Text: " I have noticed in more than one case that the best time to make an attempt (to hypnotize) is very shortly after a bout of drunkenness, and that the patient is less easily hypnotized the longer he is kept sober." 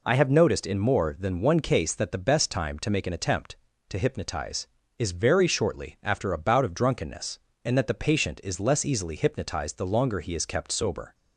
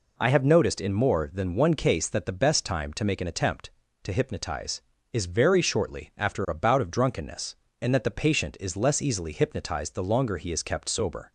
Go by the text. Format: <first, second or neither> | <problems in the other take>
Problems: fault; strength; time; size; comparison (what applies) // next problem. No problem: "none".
neither | none